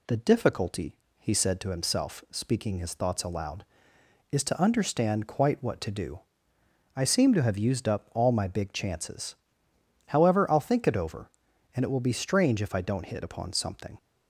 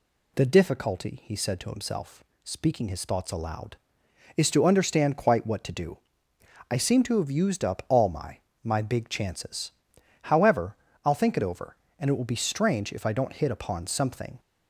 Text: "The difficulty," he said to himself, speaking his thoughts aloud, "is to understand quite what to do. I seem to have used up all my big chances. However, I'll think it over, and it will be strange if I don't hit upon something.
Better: first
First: none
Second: says "my" twice; at 8.6 s

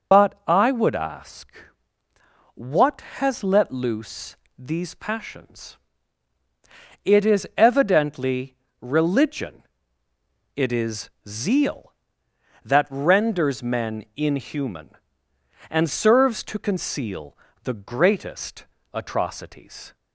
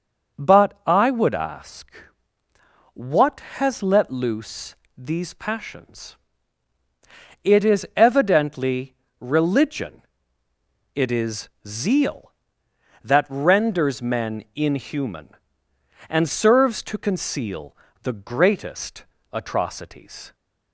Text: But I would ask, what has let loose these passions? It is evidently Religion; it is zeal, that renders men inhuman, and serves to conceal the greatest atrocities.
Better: second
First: loses the start of "But"; at 0.1 s; 135 ms // pauses between "loose" and "these"; slight; at 4.3 s; 0.22 s long // pauses between "evidently" and "Religion"; slight; at 8.5 s; 0.30 s long // pauses between "is" and "zeal"; slight; at 11.0 s; 0.18 s long // pauses between "conceal" and "the"; slight; at 17.3 s; 0.28 s long // pauses between "greatest" and "atrocities"; slight; at 18.6 s; 0.28 s long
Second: pauses between "loose" and "these"; slight; at 4.7 s; 0.22 s long // pauses between "evidently" and "Religion"; slight; at 8.9 s; 0.30 s long // pauses between "is" and "zeal"; slight; at 11.4 s; 0.18 s long // pauses between "conceal" and "the"; slight; at 17.7 s; 0.28 s long // pauses between "greatest" and "atrocities"; slight; at 19.0 s; 0.28 s long

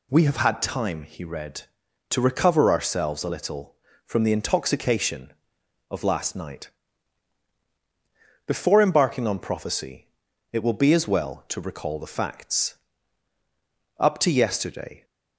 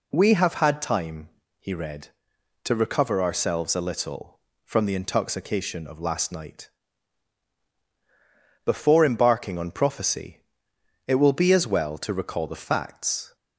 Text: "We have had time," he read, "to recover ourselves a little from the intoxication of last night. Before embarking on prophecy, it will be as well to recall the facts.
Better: second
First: goes on to say "Up to yesterday"; noticeable; from 13.9 s on; 1.0 s long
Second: none

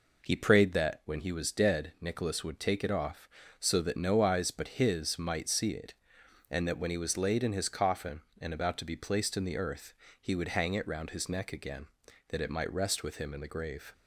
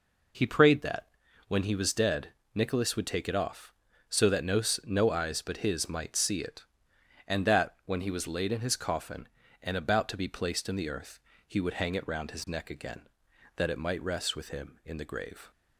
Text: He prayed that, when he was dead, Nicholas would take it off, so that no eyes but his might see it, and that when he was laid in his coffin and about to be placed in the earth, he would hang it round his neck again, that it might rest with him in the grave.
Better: first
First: none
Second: says "no" twice; at 4.8 s

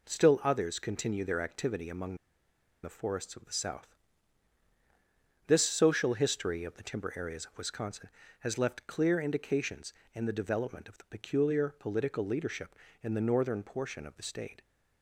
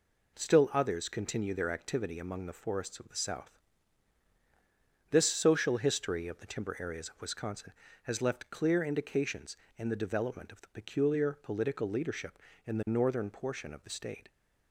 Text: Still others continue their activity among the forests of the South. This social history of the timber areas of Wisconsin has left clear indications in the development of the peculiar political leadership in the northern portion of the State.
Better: second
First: pauses between "among" and "the"; noticeable; at 2.1 s; 0.67 s long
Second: none

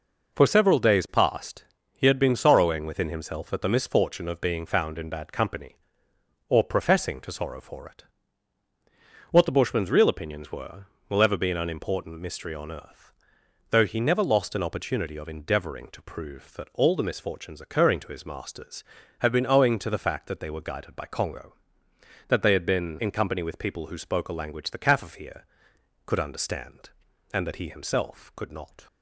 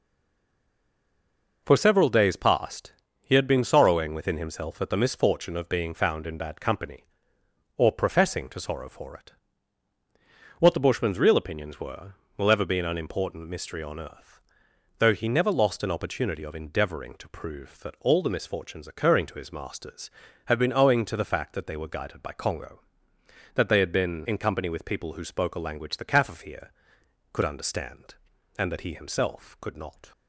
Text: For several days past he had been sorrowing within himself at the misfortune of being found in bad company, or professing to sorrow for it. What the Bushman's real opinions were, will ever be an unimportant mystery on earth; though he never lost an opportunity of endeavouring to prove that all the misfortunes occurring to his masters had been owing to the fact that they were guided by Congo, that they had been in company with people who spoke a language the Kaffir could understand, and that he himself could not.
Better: first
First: pauses between "past" and "he"; slight; at 1.6 s; 0.34 s long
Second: stays silent before the first word; noticeable; until 1.6 s; 1.6 s long // pauses between "past" and "he"; slight; at 2.9 s; 0.34 s long

